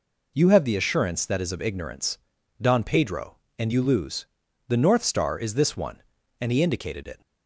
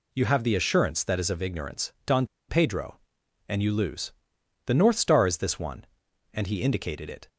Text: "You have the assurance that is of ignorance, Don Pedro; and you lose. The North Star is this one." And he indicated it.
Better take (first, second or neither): first